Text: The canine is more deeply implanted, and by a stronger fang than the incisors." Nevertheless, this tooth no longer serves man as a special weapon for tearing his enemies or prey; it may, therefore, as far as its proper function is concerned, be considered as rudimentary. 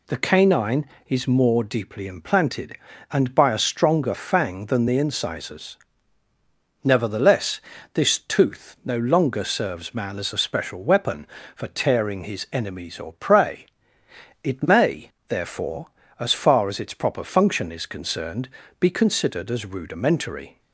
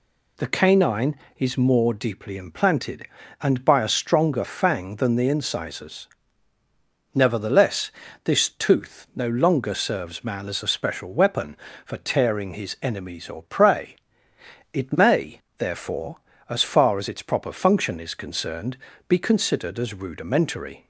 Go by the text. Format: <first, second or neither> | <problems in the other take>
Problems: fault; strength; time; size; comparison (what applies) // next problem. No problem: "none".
neither | none